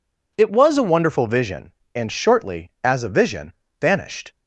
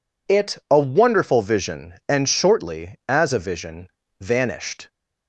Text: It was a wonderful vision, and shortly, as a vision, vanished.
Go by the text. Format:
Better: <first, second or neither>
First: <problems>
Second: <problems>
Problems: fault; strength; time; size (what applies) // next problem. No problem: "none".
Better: first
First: none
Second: skips "was"; at 0.6 s